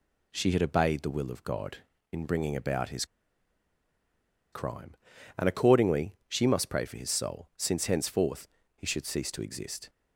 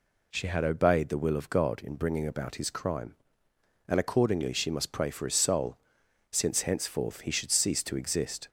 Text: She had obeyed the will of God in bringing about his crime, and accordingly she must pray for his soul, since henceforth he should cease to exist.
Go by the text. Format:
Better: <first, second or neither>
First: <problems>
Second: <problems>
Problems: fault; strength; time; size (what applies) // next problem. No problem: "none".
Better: second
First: pauses between "his" and "crime"; strong; at 3.0 s; 1.4 s long // pauses between "henceforth" and "he"; slight; at 8.4 s; 0.28 s long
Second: none